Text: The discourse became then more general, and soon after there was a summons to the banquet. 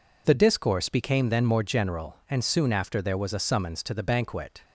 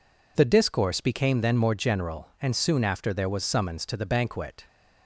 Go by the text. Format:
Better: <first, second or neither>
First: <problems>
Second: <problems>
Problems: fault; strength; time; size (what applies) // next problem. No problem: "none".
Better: first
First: none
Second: skips "a"; at 3.4 s